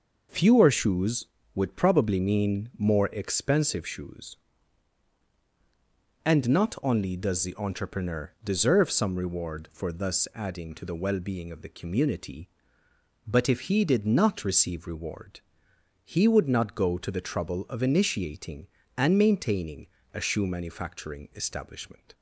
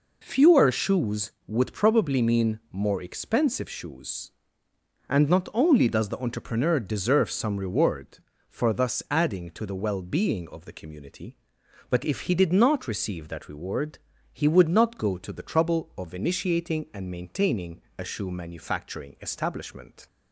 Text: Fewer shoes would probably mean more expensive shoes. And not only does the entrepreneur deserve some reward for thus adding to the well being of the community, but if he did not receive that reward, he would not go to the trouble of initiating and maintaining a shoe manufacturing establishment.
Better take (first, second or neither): second